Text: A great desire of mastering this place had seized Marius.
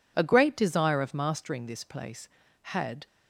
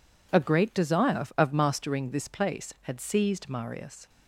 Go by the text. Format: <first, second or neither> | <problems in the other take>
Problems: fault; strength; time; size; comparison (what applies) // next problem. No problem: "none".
second | stops before "seized Marius"; at 3.0 s